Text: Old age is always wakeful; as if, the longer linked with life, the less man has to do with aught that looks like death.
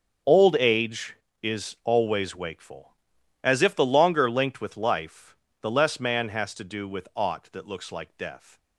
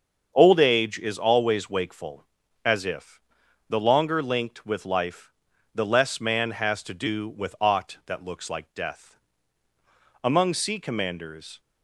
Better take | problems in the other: first | starts louder than the rest; until 1.3 s; 7 dB; also in the first // goes on to say "Among sea commanders"; from 10.2 s on; 1.3 s long

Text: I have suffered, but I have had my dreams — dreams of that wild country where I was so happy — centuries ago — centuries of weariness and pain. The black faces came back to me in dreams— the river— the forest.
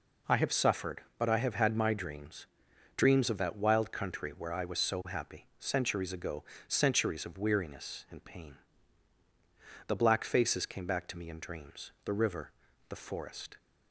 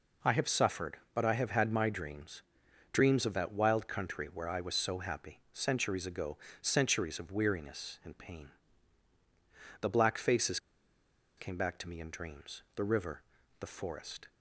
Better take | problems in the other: first | pauses between "faces" and "came"; noticeable; at 10.5 s; 0.77 s long

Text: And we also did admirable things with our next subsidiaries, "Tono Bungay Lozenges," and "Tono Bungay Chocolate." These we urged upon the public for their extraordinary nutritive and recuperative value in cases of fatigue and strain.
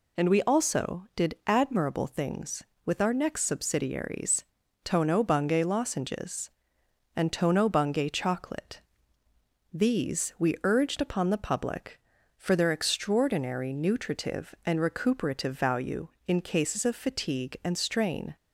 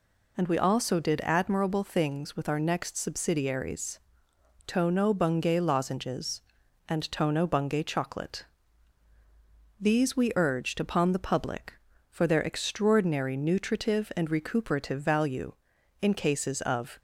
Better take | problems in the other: first | stops before "fatigue and strain"; at 16.9 s

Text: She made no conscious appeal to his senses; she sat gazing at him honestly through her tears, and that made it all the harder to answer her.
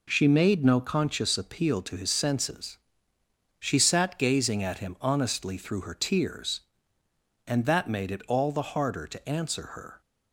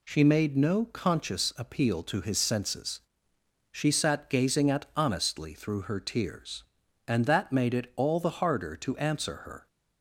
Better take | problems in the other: first | skips "him"; at 4.9 s

